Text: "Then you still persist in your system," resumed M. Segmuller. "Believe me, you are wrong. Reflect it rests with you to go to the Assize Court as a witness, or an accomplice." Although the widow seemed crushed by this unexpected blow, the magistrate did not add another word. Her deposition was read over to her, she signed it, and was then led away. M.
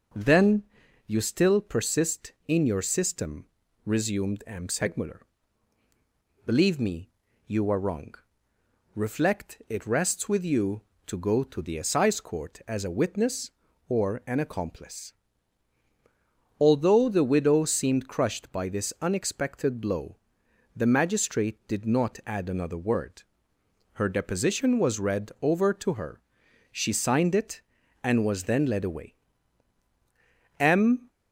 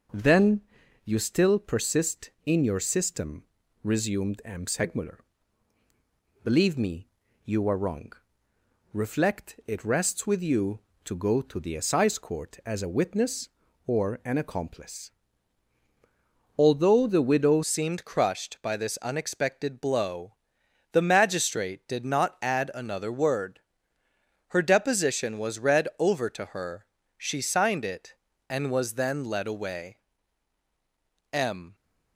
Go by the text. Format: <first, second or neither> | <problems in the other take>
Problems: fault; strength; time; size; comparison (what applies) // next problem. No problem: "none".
first | starts louder than the rest; until 1.5 s; 6 dB; also in the first // pauses between "Then" and "you"; at 0.6 s; 0.42 s long; also in the first // changes voice at "seemed"; from 17.6 s on; 14.1 s long